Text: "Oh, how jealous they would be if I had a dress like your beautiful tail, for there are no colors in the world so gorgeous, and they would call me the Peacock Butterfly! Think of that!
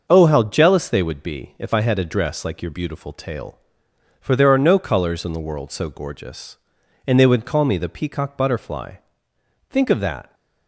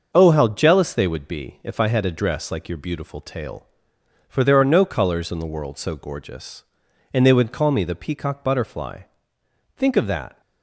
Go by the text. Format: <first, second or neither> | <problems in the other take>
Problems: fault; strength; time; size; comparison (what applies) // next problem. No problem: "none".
neither | starts louder than the rest; the same in both